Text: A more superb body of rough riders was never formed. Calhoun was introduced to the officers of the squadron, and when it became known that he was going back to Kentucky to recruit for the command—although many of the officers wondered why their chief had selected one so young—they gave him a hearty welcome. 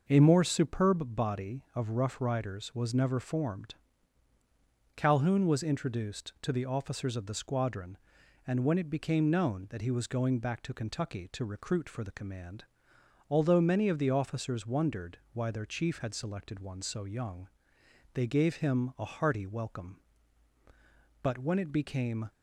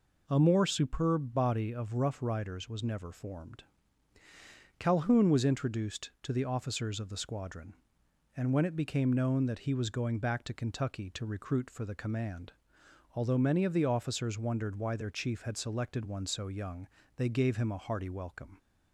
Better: second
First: starts louder than the rest; noticeable; until 1.0 s; 6 dB // goes on to say "But when it became"; noticeable; from 21.2 s on; 1.0 s long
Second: none

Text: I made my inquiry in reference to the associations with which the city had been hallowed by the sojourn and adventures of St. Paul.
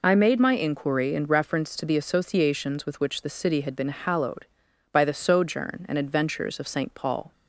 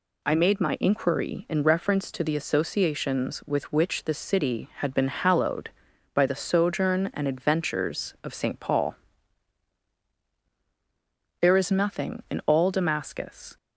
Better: first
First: none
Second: goes on to say "There is nothing in all Damascus"; strong; from 11.4 s on; 2.1 s long

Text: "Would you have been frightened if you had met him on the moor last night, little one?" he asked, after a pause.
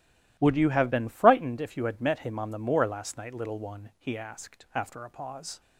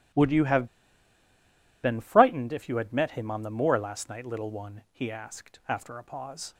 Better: first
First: starts louder than the rest; strong; until 1.4 s; 14.5 dB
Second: starts louder than the rest; strong; until 2.3 s; 14.5 dB // pauses between "have" and "been"; at 0.6 s; 1.1 s long

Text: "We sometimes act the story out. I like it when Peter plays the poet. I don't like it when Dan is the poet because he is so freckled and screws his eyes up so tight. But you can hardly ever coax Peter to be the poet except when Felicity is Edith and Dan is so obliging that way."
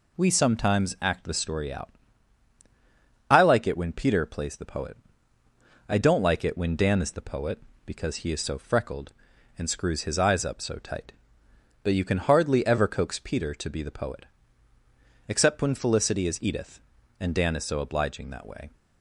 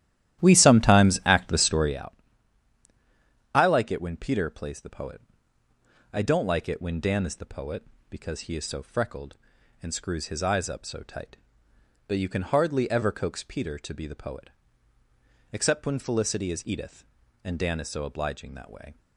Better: first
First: pauses between "poet" and "except"; at 14.2 s; 1.0 s long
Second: starts louder than the rest; strong; until 2.0 s; 12.5 dB // pauses between "poet" and "except"; at 14.5 s; 1.0 s long

